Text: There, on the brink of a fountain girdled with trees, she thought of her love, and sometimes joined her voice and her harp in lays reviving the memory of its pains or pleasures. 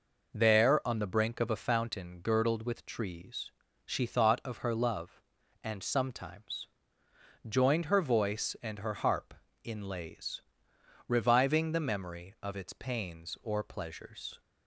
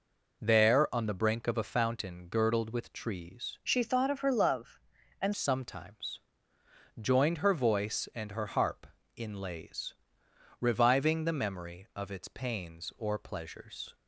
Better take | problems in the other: first | changes voice from "she" to "and"; from 3.6 to 5.3 s; 1.7 s long // pauses between "sometimes" and "joined"; noticeable; at 6.2 s; 0.78 s long; noticeable in the first // pauses between "lays" and "reviving"; noticeable; at 9.9 s; 0.68 s long; noticeable in the first

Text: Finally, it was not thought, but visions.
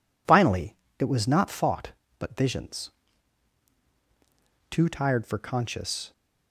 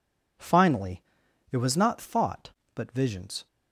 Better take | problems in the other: second | goes on to say "Too tired for conscious"; from 4.7 s on; 1.4 s long

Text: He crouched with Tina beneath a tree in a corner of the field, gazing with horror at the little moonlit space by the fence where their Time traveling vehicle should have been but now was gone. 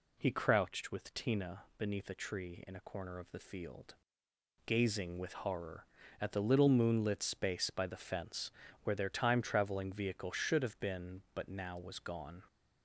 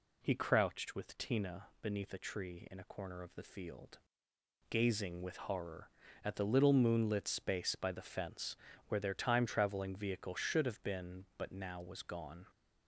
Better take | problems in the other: neither | pauses between "fence" and "where"; slight; the same in both

